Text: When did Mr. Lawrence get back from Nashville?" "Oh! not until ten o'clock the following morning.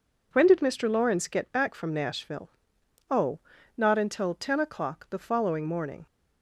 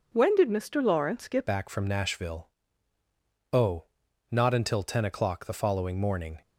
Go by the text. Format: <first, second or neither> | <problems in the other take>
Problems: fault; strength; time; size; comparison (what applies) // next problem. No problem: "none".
first | changes voice at "back"; from 1.4 s on; 5.0 s long